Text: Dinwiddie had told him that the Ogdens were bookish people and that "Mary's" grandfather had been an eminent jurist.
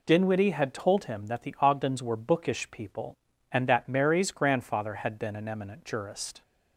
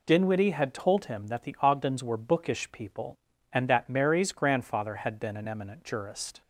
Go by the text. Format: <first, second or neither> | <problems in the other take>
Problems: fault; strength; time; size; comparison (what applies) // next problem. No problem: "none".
neither | none